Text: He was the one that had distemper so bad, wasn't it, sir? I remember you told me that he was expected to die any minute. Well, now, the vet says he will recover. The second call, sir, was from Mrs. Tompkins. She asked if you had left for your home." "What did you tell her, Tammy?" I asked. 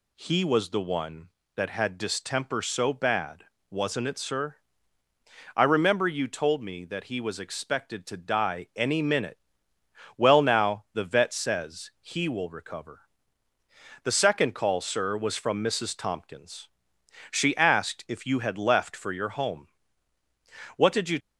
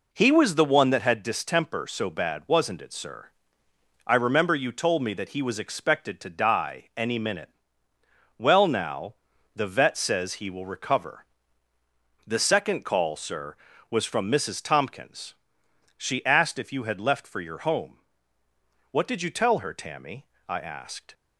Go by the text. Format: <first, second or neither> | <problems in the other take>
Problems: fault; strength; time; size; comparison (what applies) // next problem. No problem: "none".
second | stops before "tell her Tammy I asked"; at 21.1 s